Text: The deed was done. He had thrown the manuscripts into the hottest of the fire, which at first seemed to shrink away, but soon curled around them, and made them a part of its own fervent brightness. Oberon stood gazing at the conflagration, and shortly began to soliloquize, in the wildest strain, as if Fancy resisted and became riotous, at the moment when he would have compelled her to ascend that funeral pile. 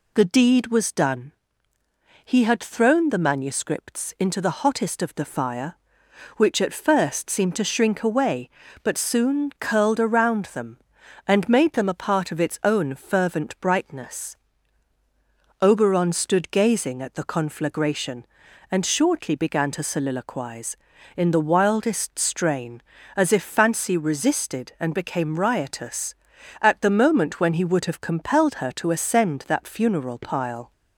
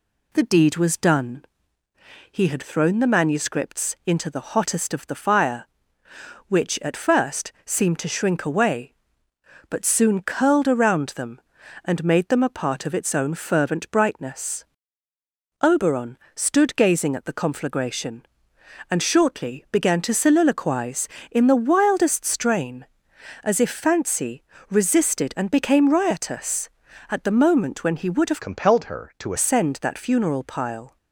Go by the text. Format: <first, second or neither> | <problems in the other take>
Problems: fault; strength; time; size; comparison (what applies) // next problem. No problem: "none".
first | pauses between "Oberon" and "stood"; slight; at 16.1 s; 0.18 s long // pauses between "Fancy" and "resisted"; slight; at 24.4 s; 0.28 s long // changes voice from "compelled" to "to"; from 28.4 to 29.3 s; 0.9 s long